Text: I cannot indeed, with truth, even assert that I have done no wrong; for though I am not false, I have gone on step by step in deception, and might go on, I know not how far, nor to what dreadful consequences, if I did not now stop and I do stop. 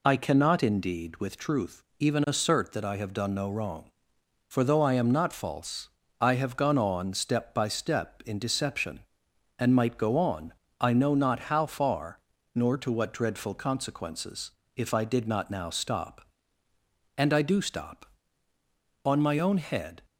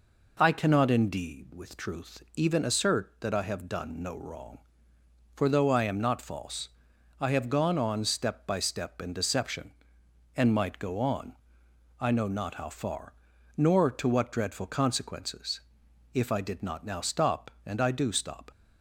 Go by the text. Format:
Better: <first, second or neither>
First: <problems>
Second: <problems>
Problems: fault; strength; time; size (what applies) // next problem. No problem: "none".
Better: second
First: goes on to say "On my own head"; noticeable; from 19.0 s on; 0.96 s long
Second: none